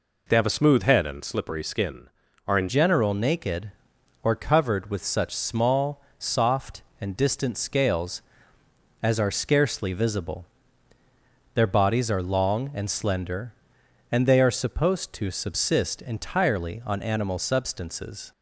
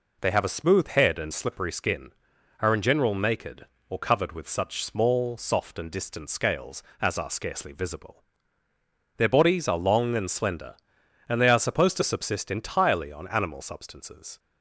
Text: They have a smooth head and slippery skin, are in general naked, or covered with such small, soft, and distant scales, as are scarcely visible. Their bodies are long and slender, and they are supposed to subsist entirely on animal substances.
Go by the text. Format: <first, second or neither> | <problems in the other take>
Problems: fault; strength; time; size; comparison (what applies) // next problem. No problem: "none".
second | changes voice at "general"; from 2.6 s on; 15.7 s long